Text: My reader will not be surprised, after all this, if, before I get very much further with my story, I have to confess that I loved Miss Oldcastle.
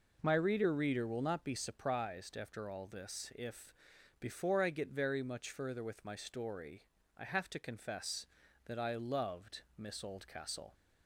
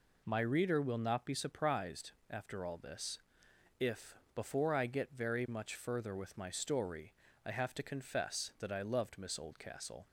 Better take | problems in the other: second | says "reader" twice; at 0.7 s // pauses between "loved" and "Miss"; slight; at 9.6 s; 0.16 s long

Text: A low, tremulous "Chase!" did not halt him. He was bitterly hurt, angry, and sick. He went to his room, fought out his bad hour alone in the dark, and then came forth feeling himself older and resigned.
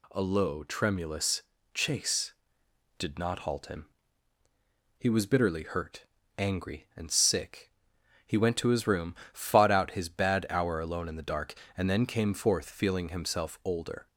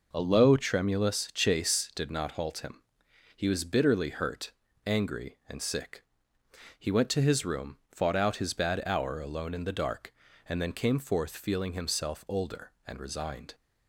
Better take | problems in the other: second | pauses between "tremulous" and "Chase"; slight; at 1.4 s; 0.32 s long // stops before "and resigned"; at 14.0 s

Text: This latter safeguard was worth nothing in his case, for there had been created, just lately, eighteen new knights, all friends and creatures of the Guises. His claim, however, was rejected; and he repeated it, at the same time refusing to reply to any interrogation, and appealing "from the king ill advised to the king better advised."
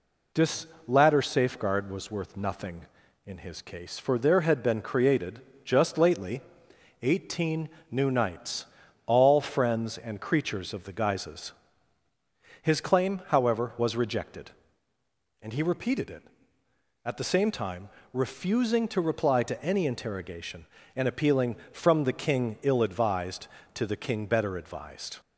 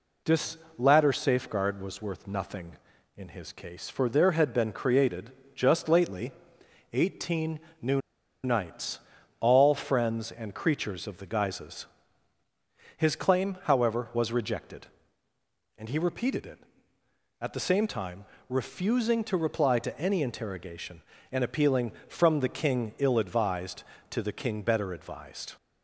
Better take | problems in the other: first | pauses between "This" and "latter"; slight; at 0.5 s; 0.20 s long; slight in the first // pauses between "eighteen" and "new"; slight; at 7.5 s; 0.22 s long; slight in the first // pauses between "new" and "knights"; at 8.0 s; 0.43 s long // pauses between "time" and "refusing"; slight; at 18.2 s; 0.24 s long; slight in the first

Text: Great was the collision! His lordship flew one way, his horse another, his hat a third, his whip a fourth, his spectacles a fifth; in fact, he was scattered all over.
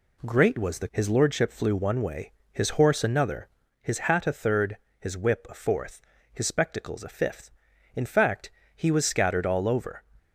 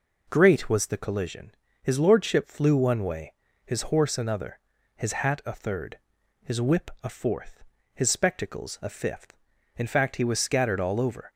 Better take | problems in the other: second | skips "collision"; at 0.8 s

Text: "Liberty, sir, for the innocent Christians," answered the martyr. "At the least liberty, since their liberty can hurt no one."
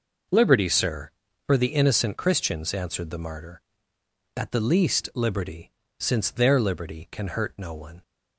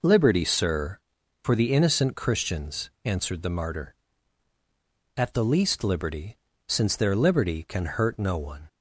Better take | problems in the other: neither | none

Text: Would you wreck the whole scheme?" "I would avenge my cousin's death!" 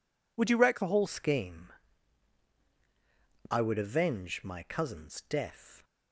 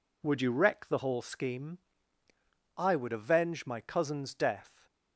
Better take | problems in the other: second | changes voice at "scheme"; from 1.0 s on; 4.8 s long

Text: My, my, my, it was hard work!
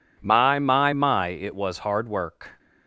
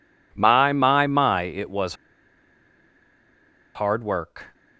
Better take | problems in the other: first | pauses between "was" and "hard"; strong; at 1.9 s; 1.8 s long

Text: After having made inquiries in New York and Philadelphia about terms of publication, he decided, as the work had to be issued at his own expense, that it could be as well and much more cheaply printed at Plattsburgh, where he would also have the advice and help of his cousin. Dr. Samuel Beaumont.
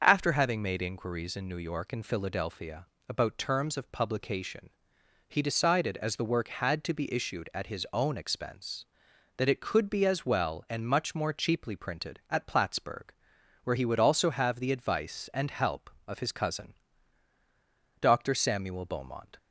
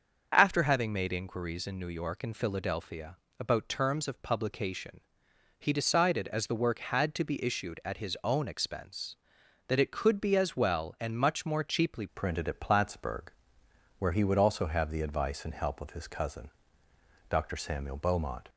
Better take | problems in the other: first | starts louder than the rest; until 1.3 s; 6.5 dB; also in the first // pauses between "Philadelphia" and "about"; slight; at 3.1 s; 0.22 s long; slight in the first // changes voice at "printed"; from 12.1 s on; 6.3 s long

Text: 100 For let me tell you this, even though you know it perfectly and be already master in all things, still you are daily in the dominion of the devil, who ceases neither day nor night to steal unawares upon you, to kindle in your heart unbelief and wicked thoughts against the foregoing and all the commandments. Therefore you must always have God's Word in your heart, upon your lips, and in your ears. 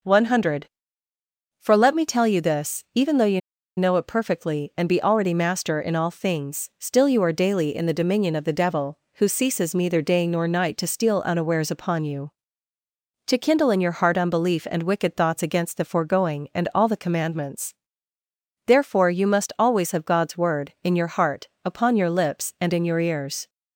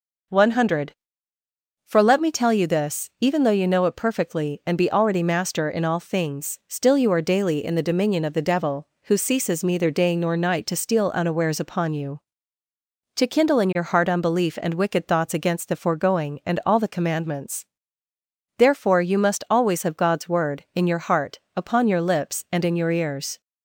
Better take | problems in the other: second | pauses between "you" and "know"; at 3.4 s; 0.36 s long

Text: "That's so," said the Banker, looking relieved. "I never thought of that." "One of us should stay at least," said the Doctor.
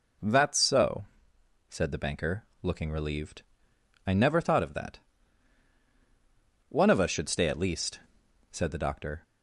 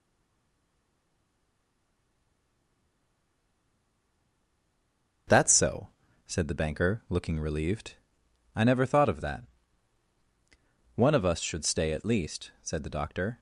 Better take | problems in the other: first | stays silent before the first word; strong; until 5.2 s; 5.2 s long // starts louder than the rest; noticeable; until 6.6 s; 6 dB

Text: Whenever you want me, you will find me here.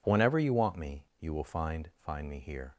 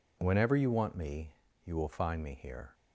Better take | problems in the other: second | says "find" twice; at 2.0 s

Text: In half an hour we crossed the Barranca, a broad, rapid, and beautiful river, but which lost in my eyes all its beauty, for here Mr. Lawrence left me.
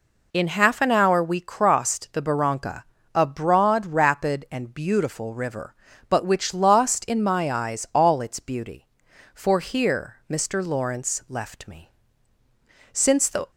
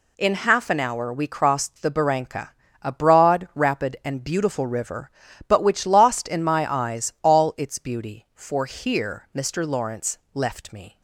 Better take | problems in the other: second | goes on to say "Since the"; from 12.9 s on; 0.58 s long

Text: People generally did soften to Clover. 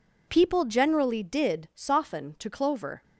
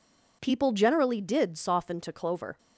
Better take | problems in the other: neither | none

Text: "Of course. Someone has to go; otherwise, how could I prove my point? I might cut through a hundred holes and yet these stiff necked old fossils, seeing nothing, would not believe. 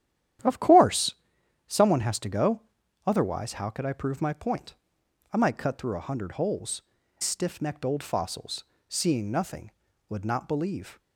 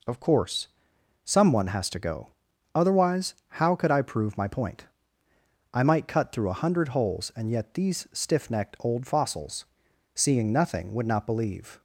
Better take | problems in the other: second | starts louder than the rest; strong; until 1.9 s; 11 dB // skips "and yet these"; at 7.0 s

